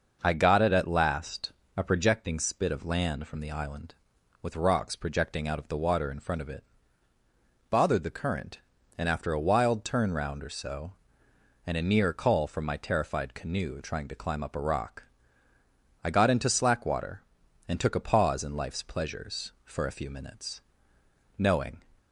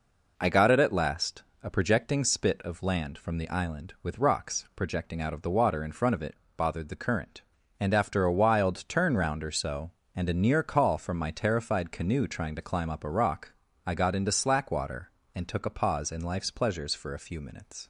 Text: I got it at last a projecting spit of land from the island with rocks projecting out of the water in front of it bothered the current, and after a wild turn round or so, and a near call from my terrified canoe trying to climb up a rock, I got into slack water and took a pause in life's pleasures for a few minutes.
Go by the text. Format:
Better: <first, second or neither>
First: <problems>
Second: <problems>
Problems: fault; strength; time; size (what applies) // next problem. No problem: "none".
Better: second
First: starts louder than the rest; noticeable; until 1.2 s; 6 dB // pauses between "last" and "a"; slight; at 1.5 s; 0.26 s long // pauses between "it" and "bothered"; at 6.6 s; 1.0 s long // goes on to say "Knowing"; slight; from 21.3 s on; 0.42 s long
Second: pauses between "last" and "a"; slight; at 1.4 s; 0.20 s long // pauses between "it" and "bothered"; slight; at 6.3 s; 0.22 s long